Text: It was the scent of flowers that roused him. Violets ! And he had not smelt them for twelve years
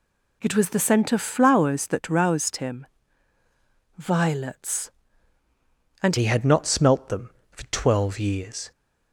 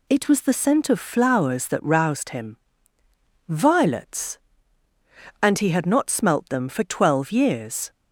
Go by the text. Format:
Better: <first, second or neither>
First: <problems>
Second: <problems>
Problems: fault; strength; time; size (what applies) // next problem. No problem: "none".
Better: second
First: changes voice at "he"; from 6.1 s on; 2.6 s long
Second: none